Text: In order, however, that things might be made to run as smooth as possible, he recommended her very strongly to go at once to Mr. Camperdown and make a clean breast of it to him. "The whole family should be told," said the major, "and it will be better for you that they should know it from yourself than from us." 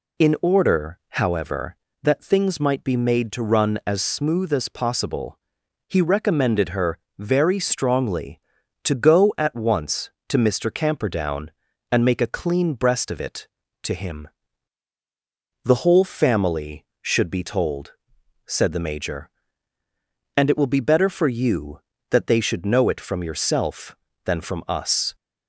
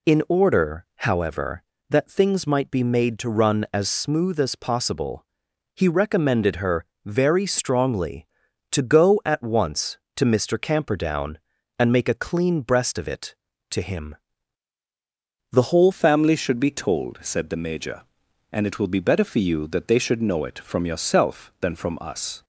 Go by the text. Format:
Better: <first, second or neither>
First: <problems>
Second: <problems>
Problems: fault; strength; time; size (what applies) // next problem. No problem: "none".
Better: first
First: pauses between "her" and "very"; slight; at 6.9 s; 0.20 s long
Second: pauses between "her" and "very"; slight; at 6.8 s; 0.20 s long // changes voice at "family"; from 15.9 s on; 6.5 s long